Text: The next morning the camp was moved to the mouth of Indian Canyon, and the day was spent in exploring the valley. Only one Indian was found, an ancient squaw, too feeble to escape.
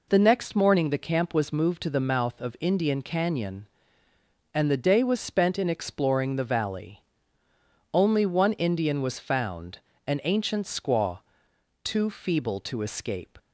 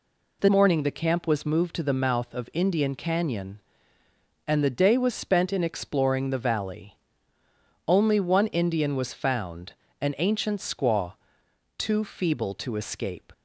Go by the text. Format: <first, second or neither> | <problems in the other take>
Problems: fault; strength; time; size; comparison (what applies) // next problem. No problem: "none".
first | skips "next"; at 0.4 s